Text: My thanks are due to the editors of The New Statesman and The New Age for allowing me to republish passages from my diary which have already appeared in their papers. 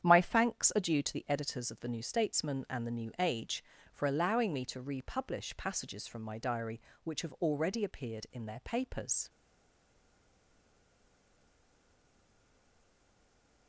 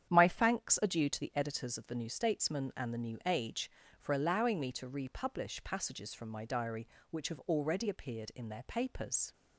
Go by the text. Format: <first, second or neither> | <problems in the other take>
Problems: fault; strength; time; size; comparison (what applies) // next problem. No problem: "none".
second | starts louder than the rest; strong; until 1.0 s; 9 dB; strong in the second // stays silent after the last word; strong; from 9.2 s on; 4.4 s long